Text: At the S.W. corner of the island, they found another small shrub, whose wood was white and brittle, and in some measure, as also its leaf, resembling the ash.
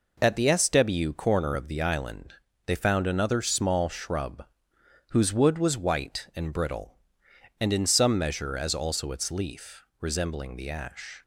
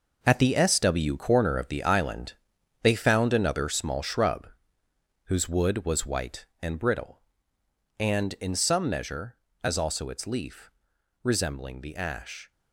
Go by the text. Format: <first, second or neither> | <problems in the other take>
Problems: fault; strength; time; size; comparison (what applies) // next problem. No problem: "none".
first | gets quieter; strong; throughout; 10.5 dB